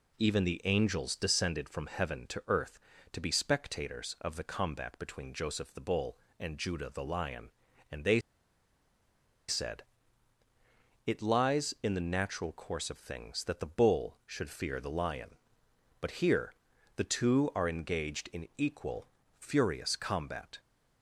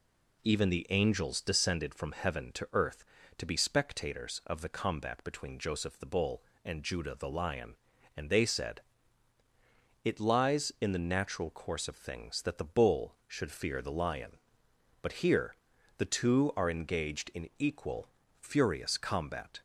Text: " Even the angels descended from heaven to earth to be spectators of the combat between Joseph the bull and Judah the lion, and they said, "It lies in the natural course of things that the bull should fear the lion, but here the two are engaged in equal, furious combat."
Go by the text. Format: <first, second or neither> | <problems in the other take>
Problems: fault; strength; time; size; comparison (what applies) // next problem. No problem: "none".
second | pauses between "they" and "said"; strong; at 8.2 s; 1.2 s long // pauses between "here" and "the"; at 16.5 s; 0.42 s long; also in the second